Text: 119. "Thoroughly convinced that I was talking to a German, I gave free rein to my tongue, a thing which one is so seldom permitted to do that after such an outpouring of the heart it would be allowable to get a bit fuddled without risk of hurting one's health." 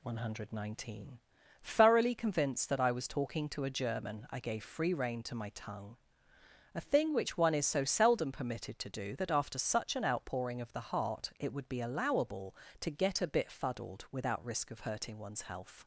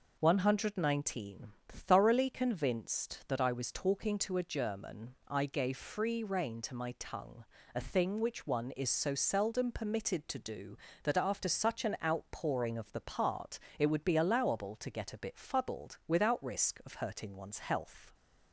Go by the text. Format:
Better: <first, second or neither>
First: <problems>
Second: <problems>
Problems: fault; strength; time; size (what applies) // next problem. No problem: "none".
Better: first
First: none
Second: says "part" for "heart"; at 13.0 s